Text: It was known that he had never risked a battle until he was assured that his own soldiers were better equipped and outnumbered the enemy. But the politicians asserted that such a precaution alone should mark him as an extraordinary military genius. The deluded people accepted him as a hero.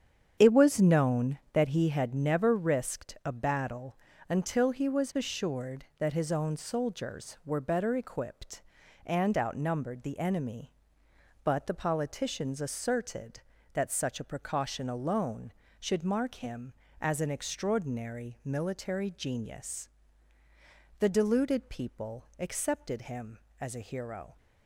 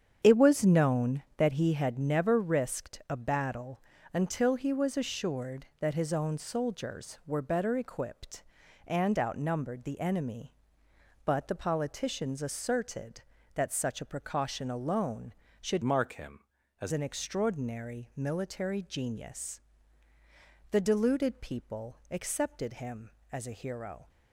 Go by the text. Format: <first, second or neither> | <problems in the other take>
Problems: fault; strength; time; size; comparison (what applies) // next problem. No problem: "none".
first | starts louder than the rest; strong; until 1.2 s; 8 dB; strong in the first // pauses between "battle" and "until"; slight; at 3.8 s; 0.32 s long; slight in the first // changes voice from "mark" to "as"; from 15.8 to 16.9 s; 1.1 s long